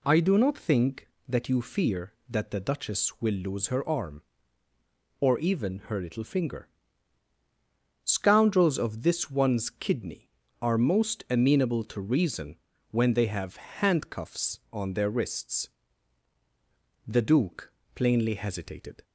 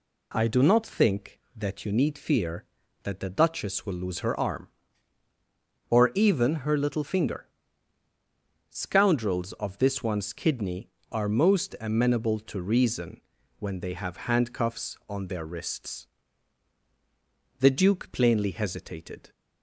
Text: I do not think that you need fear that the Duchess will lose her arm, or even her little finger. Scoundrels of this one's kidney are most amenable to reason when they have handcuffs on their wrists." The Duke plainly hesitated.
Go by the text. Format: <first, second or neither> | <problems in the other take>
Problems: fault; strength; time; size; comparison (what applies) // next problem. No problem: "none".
second | skips "need"; at 1.6 s // pauses between "reason" and "when"; slight; at 12.5 s; 0.34 s long; also in the second // pauses between "Duke" and "plainly"; slight; at 17.7 s; 0.22 s long